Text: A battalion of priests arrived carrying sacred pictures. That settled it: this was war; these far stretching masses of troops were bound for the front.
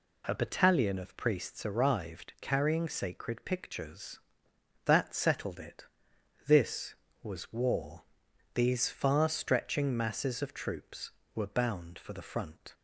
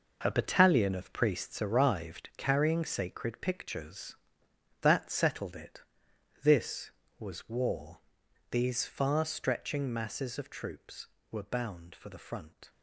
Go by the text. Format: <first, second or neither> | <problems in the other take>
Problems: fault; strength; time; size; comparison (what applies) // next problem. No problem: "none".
first | gets quieter; strong; throughout; 10.5 dB